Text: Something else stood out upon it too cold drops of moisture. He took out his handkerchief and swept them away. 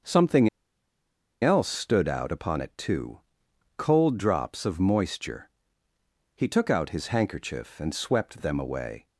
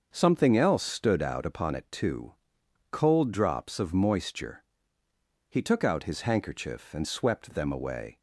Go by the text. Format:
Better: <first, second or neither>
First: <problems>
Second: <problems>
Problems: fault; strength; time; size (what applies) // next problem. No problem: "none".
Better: second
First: starts louder than the rest; until 1.9 s; 6.5 dB // pauses between "Something" and "else"; noticeable; at 0.4 s; 0.93 s long // pauses between "too" and "cold"; noticeable; at 3.1 s; 0.56 s long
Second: starts louder than the rest; until 1.1 s; 6.5 dB // pauses between "too" and "cold"; noticeable; at 2.3 s; 0.56 s long